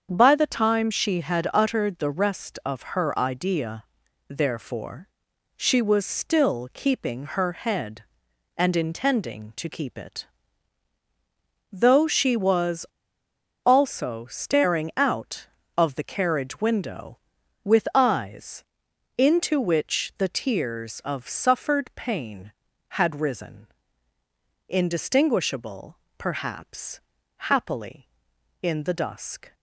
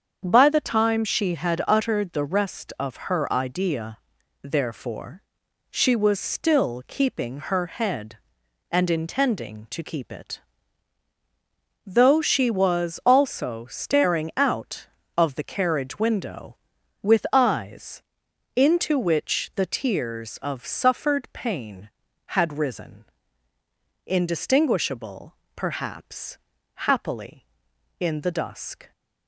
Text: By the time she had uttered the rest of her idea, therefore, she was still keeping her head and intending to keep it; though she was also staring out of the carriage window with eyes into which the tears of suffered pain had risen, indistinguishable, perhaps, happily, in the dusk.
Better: second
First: starts louder than the rest; strong; until 1.1 s; 7.5 dB // pauses between "was" and "also"; noticeable; at 12.8 s; 0.78 s long // pauses between "eyes" and "into"; noticeable; at 18.6 s; 0.54 s long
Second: starts louder than the rest; strong; until 1.2 s; 7.5 dB // pauses between "eyes" and "into"; noticeable; at 18.0 s; 0.54 s long

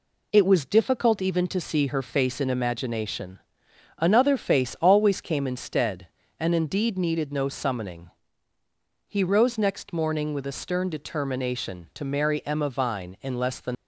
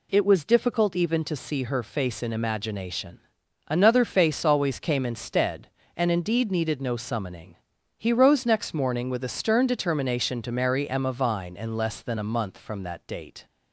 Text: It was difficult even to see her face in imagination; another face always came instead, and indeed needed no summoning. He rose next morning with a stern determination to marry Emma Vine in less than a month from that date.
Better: second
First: stops before "a month from that date"; at 13.7 s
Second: none

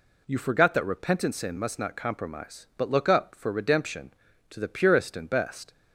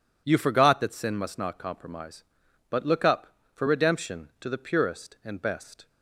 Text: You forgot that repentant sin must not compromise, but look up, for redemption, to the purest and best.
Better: first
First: none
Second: skips "repentant"; at 0.9 s

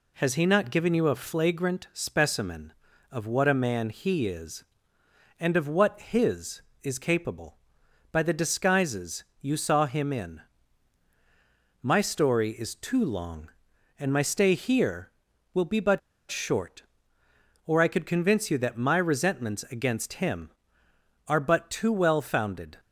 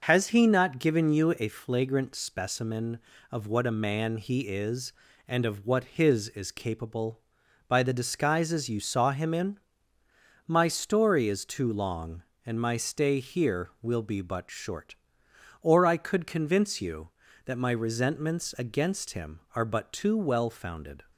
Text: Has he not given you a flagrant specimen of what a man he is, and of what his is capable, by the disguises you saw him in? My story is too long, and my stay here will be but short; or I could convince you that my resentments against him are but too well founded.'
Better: second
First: pauses between "disguises" and "you"; slight; at 9.2 s; 0.16 s long // pauses between "but" and "short"; slight; at 15.9 s; 0.29 s long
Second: none

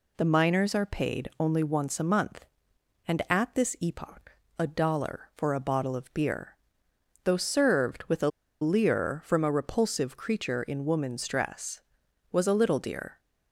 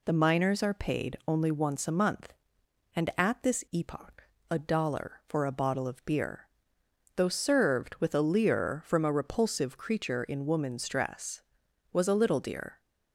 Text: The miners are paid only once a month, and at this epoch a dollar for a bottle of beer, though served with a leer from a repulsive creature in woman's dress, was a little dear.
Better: second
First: pauses between "epoch" and "a"; slight; at 4.3 s; 0.26 s long // pauses between "a" and "leer"; slight; at 8.2 s; 0.32 s long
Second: pauses between "epoch" and "a"; slight; at 4.2 s; 0.26 s long

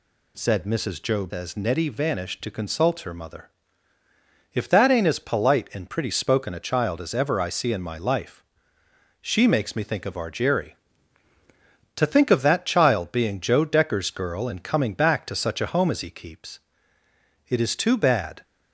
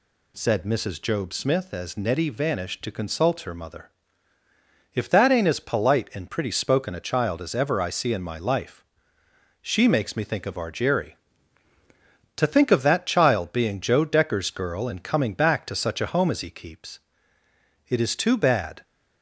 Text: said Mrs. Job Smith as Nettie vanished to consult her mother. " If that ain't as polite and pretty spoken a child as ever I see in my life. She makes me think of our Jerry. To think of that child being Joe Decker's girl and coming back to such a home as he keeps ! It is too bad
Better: second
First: skips "Smith"; at 1.3 s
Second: none

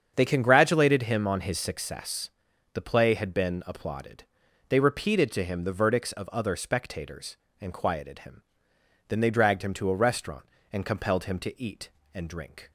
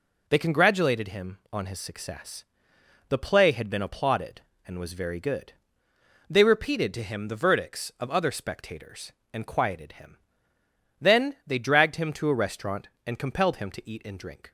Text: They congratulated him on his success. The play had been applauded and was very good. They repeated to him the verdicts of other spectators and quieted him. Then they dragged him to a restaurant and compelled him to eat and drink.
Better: second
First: starts louder than the rest; strong; until 1.1 s; 7.5 dB // skips "and was very good"; at 4.4 s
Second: none

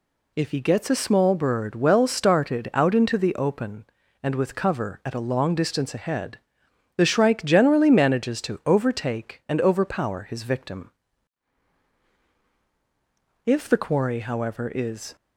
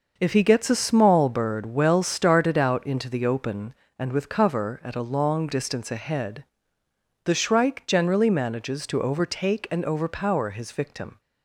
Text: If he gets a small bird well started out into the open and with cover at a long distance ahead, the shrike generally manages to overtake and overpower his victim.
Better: second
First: goes on to say "If the quarry however is"; strong; from 13.4 s on; 1.7 s long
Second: none

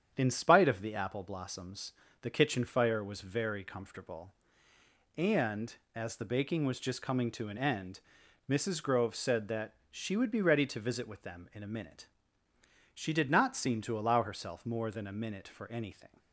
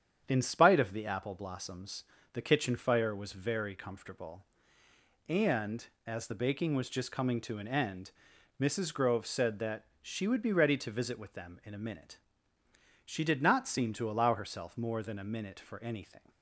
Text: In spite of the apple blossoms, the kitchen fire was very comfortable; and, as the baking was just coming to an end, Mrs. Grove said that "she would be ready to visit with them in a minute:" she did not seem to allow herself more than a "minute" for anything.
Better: neither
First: starts louder than the rest; strong; until 1.1 s; 8.5 dB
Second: starts louder than the rest; strong; until 1.2 s; 8.5 dB

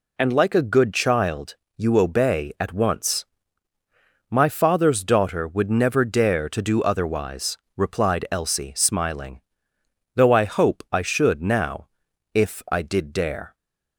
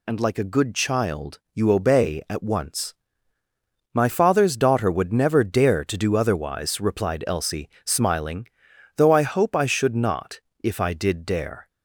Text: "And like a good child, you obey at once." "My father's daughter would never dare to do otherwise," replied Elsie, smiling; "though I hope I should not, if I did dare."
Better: second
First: says "now" for "not"; at 11.4 s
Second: none

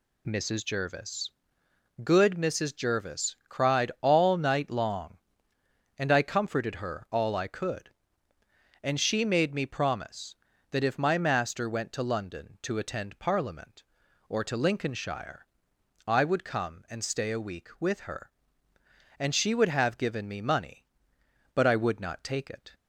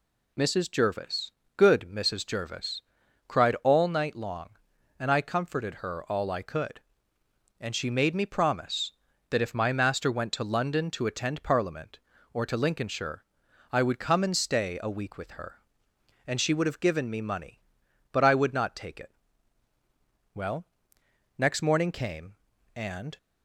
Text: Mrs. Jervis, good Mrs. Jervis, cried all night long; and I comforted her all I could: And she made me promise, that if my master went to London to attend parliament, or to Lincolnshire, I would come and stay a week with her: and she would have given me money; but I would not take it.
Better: first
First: none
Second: goes on to say "Well next morning came and"; strong; from 20.3 s on; 2.8 s long

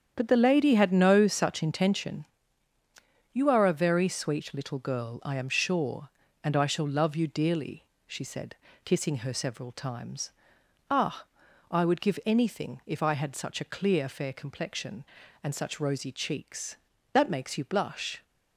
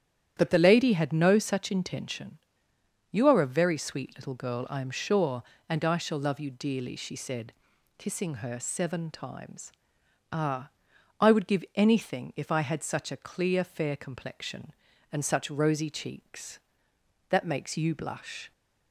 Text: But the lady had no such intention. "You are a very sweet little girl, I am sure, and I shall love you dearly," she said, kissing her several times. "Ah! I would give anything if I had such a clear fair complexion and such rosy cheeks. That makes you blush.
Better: first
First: starts louder than the rest; strong; until 1.1 s; 8.5 dB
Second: starts louder than the rest; strong; until 1.3 s; 10 dB // says "seven" for "several"; at 8.5 s

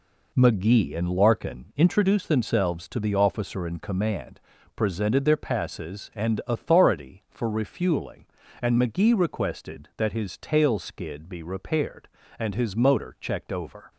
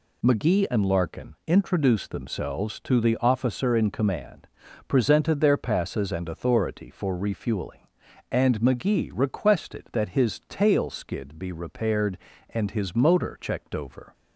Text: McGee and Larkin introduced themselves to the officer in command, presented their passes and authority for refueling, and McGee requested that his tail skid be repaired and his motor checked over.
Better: neither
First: none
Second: none

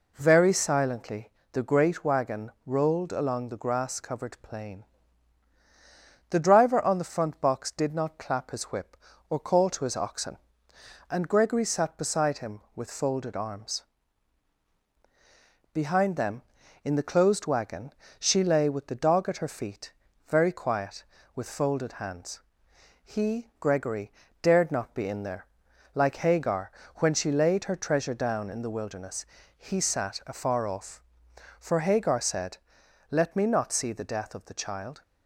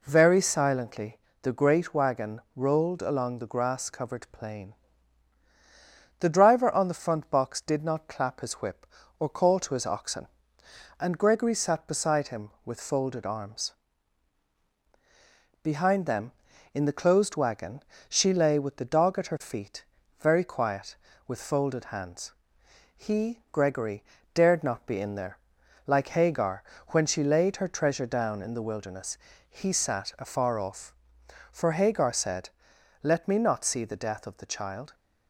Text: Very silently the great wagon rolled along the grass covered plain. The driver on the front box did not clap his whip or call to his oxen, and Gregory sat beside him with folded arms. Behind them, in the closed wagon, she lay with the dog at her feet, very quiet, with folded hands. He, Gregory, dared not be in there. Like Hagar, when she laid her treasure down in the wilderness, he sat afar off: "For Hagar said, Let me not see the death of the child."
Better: neither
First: pauses between "silently" and "the"; slight; at 1.2 s; 0.22 s long // pauses between "wagon" and "rolled"; slight; at 2.4 s; 0.16 s long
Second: pauses between "silently" and "the"; slight; at 1.1 s; 0.24 s long // pauses between "wagon" and "rolled"; slight; at 2.3 s; 0.16 s long

